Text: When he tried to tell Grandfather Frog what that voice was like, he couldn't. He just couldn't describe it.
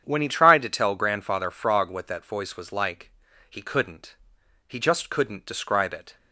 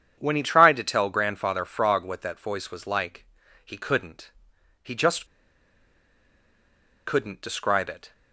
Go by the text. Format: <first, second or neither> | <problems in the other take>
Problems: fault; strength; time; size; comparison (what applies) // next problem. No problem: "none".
first | starts louder than the rest; strong; until 1.2 s; 8.5 dB; strong in the first // pauses between "just" and "couldn't"; strong; at 5.2 s; 1.8 s long